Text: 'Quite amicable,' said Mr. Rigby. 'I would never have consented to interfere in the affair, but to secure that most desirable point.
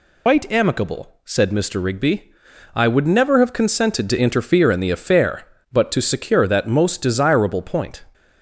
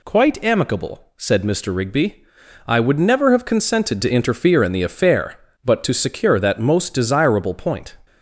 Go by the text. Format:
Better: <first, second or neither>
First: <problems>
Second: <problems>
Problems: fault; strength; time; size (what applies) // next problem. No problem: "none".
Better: second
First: loses the start of "Quite"; at 0.2 s; 140 ms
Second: none